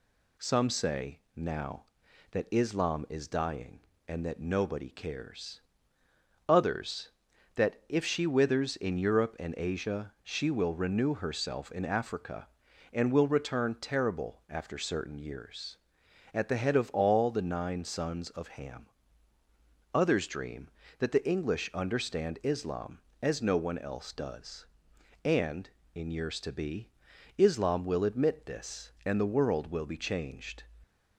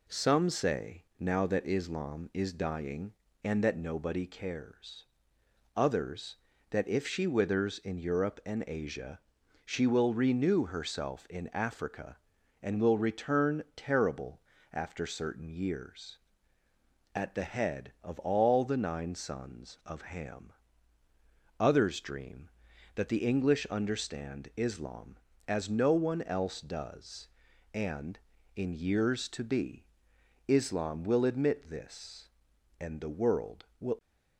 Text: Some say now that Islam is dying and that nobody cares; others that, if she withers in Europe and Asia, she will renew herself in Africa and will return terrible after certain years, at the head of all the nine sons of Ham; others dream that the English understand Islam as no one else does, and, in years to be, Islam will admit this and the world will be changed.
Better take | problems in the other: first | pauses between "say" and "now"; slight; at 1.0 s; 0.16 s long; slight in the first // pauses between "terrible" and "after"; slight; at 14.3 s; 0.32 s long // stops before "be changed"; at 33.9 s

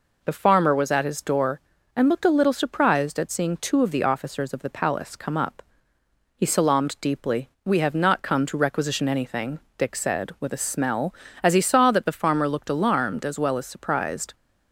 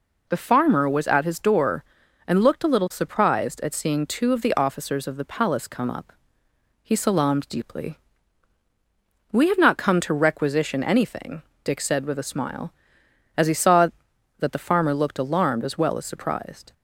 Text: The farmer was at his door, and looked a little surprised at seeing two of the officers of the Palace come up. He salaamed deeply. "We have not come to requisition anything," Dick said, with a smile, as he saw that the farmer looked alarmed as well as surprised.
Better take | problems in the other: second | says "smell" for "smile"; at 10.6 s

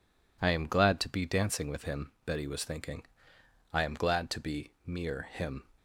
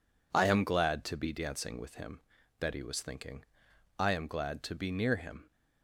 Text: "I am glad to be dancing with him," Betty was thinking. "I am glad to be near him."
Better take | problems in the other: second | says "mere" for "near"; at 4.8 s

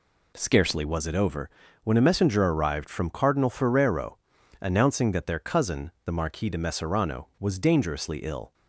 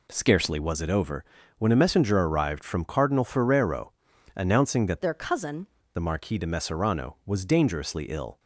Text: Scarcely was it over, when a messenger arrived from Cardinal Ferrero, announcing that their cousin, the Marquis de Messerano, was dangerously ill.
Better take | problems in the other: first | changes voice from "their" to "cousin"; from 5.0 to 5.6 s; 0.6 s long

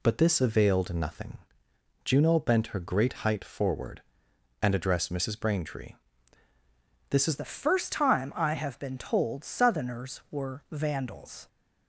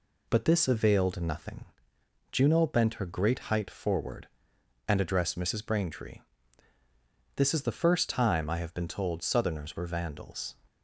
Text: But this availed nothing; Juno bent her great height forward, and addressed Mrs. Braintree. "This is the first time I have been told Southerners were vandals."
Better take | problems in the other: second | changes voice at "the"; from 7.3 s on; 4.1 s long

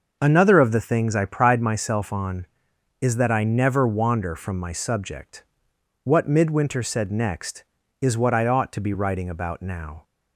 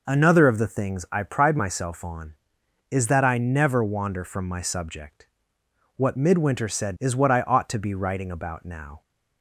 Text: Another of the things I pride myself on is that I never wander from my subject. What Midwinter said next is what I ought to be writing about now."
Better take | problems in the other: first | skips "next"; at 6.9 s

